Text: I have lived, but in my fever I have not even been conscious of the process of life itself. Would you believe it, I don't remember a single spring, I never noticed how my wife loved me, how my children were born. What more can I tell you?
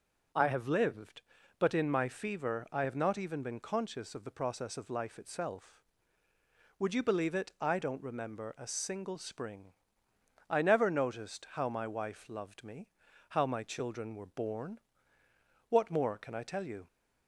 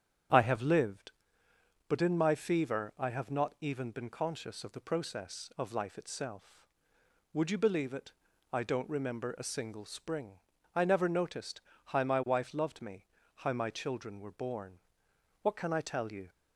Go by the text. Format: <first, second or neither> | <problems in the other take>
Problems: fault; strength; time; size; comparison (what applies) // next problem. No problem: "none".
first | starts louder than the rest; strong; until 2.1 s; 9 dB // pauses between "noticed" and "how"; slight; at 11.5 s; 0.28 s long // skips "more"; at 15.5 s